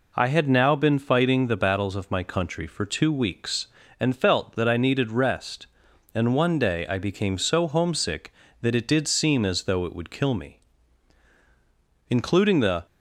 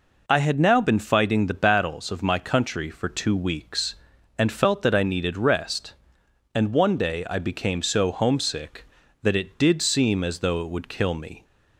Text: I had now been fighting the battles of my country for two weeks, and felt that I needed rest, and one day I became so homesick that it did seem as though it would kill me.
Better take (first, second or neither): second